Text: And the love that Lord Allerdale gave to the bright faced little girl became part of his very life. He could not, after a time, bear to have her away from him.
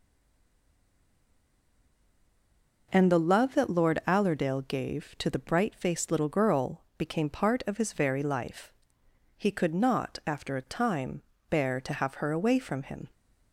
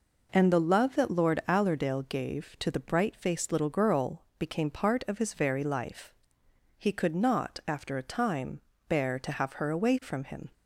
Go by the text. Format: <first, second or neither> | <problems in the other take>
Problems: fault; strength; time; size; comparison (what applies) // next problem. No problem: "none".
second | stays silent before the first word; strong; until 2.9 s; 2.9 s long // pauses between "girl" and "became"; slight; at 6.8 s; 0.16 s long; slight in the second